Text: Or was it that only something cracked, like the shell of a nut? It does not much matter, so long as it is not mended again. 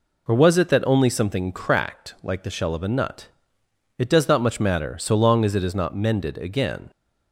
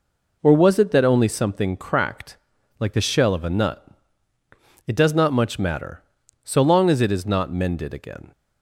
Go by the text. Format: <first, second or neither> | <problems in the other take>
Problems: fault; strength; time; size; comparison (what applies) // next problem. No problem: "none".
neither | none